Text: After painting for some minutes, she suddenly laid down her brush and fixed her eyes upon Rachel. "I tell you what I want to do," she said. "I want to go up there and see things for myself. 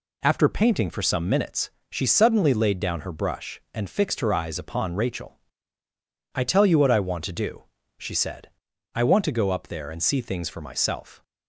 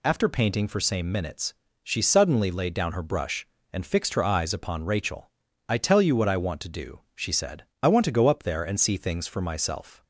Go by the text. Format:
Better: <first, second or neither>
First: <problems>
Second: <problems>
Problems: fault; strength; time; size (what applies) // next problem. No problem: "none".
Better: first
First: none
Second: says "same" for "some"; at 0.7 s